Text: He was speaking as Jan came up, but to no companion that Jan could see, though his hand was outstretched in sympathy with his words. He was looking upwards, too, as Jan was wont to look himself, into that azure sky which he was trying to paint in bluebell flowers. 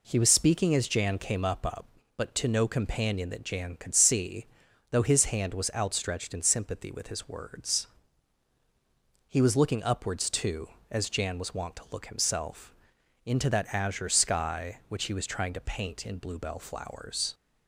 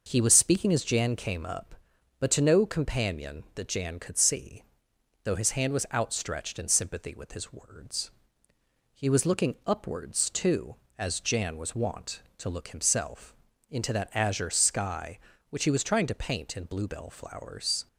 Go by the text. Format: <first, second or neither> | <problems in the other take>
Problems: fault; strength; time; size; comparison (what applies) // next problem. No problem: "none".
second | says "up" twice; at 1.6 s